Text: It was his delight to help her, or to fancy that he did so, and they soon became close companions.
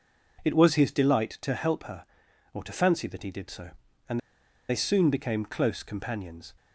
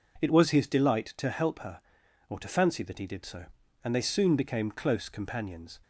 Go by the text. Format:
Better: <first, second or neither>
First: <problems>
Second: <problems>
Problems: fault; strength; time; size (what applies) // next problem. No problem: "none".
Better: second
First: pauses between "and" and "they"; noticeable; at 4.1 s; 0.49 s long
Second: none